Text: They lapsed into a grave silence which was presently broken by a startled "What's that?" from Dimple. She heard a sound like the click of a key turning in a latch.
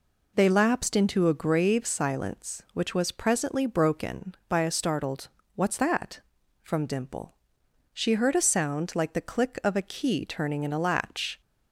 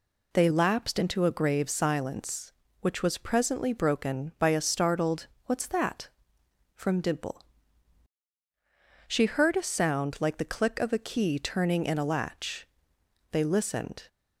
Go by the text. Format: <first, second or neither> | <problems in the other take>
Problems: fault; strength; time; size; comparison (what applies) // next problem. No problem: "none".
first | pauses between "startled" and "What's"; slight; at 5.2 s; 0.18 s long; slight in the first // goes on to say "They listened"; noticeable; from 13.2 s on; 0.78 s long